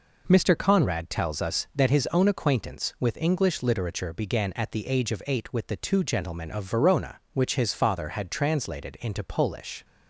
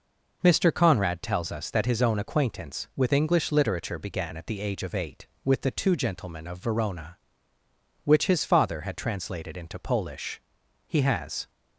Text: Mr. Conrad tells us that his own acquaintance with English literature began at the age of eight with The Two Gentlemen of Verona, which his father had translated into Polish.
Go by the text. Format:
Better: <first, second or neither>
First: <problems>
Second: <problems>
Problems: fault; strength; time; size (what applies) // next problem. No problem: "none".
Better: first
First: none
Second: goes on to say "He has"; noticeable; from 10.8 s on; 0.62 s long